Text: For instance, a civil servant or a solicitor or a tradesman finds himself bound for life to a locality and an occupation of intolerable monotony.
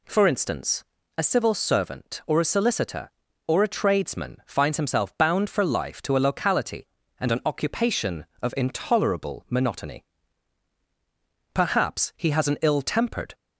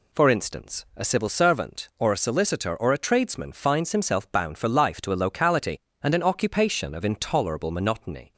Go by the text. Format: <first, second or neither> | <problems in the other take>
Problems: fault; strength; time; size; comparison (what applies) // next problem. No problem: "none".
second | goes on to say "Perhaps he has an ill tempered"; strong; from 11.5 s on; 1.8 s long